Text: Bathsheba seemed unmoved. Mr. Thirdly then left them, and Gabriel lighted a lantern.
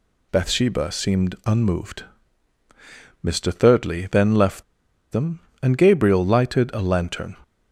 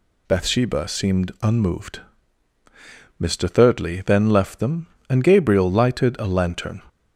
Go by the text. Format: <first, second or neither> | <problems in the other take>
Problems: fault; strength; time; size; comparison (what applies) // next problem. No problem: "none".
second | pauses between "left" and "them"; noticeable; at 4.6 s; 0.49 s long